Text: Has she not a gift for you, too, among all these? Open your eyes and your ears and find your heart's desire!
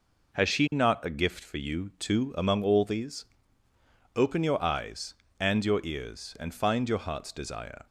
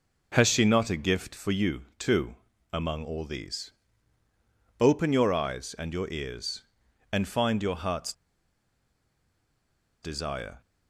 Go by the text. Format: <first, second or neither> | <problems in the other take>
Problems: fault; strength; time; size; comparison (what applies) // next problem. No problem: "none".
first | pauses between "heart's" and "desire"; strong; at 8.1 s; 1.8 s long